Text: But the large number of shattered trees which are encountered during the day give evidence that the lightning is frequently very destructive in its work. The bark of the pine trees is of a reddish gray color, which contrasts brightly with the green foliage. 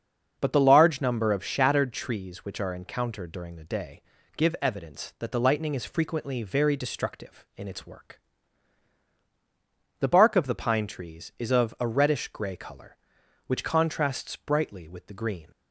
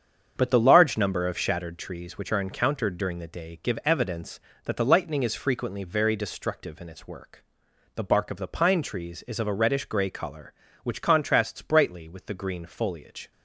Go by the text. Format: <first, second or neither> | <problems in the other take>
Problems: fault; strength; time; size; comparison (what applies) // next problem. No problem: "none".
second | starts louder than the rest; until 1.4 s; 6.5 dB; strong in the second // pauses between "day" and "give"; slight; at 4.0 s; 0.34 s long // stops before "foliage"; at 15.5 s